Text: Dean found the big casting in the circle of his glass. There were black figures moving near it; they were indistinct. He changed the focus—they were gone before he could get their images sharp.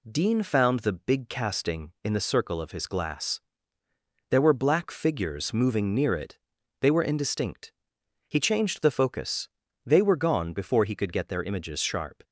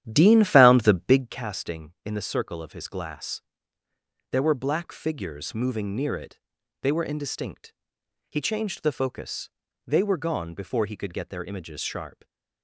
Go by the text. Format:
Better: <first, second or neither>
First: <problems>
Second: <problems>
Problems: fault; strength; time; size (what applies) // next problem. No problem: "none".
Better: first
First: none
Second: starts louder than the rest; strong; until 1.4 s; 11 dB